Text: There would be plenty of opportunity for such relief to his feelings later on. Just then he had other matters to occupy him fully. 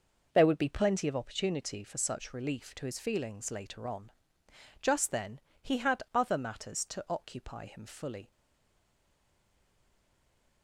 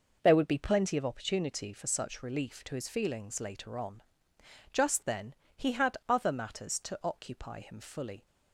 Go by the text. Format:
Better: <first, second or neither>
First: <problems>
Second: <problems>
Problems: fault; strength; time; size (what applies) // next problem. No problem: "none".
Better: second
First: pauses between "then" and "he"; slight; at 5.4 s; 0.22 s long // stays silent after the last word; from 8.3 s on; 2.3 s long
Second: pauses between "then" and "he"; slight; at 5.3 s; 0.22 s long